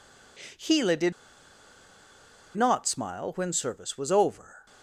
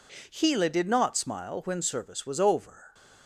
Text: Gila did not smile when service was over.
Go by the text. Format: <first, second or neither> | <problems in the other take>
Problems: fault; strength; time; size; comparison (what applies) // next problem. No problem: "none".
second | pauses between "did" and "not"; strong; at 1.1 s; 1.4 s long // stays silent after the last word; slight; from 4.3 s on; 0.5 s long; slight in the second